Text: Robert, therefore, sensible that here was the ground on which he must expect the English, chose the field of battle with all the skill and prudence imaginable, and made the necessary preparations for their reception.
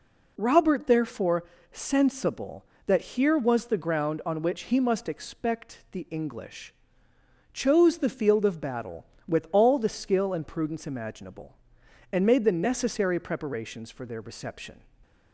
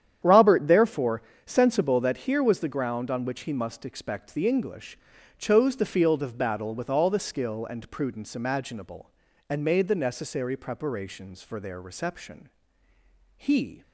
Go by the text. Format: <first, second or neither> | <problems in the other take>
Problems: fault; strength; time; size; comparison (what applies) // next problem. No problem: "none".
first | starts louder than the rest; strong; until 1.4 s; 9.5 dB // goes on to say "He"; slight; from 13.3 s on; 0.46 s long